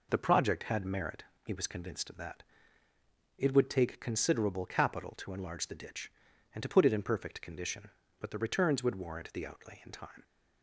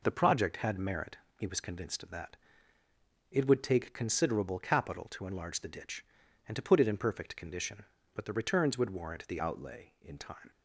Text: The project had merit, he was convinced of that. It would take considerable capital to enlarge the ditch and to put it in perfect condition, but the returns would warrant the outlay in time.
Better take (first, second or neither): first